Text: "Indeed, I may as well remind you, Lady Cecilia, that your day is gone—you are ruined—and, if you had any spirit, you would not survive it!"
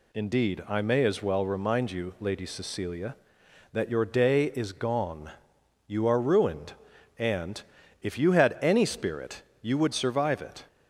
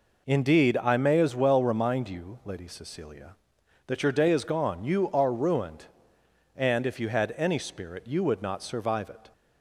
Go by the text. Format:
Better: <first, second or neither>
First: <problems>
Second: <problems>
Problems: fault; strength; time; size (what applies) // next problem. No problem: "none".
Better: second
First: skips "not"; at 9.9 s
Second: none